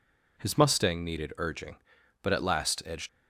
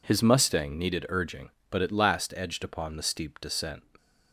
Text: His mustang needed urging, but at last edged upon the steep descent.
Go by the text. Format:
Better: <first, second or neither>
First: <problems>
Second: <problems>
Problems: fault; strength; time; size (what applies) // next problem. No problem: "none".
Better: second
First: stops before "upon the steep descent"; at 3.0 s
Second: none